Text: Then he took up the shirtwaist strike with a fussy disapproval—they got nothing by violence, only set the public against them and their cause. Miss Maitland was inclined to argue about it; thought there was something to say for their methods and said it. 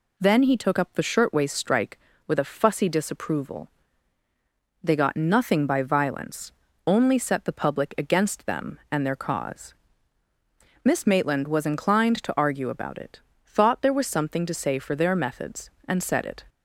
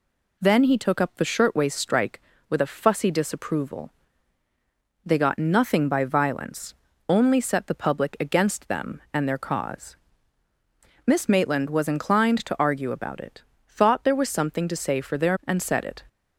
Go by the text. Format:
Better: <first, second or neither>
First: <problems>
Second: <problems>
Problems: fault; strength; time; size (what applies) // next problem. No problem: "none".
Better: first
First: none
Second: skips "methods"; at 15.4 s